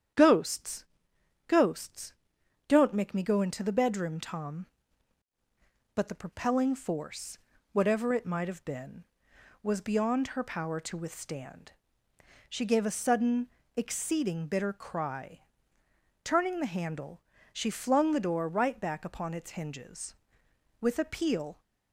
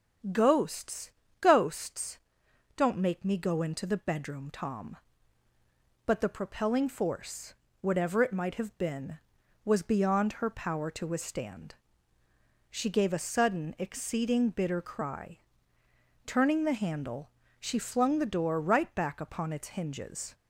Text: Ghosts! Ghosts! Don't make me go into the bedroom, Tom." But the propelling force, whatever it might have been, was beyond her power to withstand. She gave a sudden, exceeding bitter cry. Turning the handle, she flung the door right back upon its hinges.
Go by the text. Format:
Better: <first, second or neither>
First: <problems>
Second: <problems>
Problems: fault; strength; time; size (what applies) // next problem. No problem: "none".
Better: second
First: starts louder than the rest; strong; until 1.8 s; 9 dB // goes on to say "With a peal"; noticeable; from 20.8 s on; 0.80 s long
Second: starts louder than the rest; strong; until 1.6 s; 8 dB